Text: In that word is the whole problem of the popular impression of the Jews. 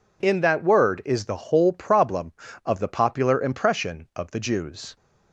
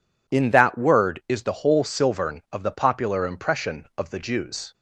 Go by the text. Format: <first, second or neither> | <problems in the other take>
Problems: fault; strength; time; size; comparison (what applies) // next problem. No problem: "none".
first | says "silvern" for "problem"; at 1.8 s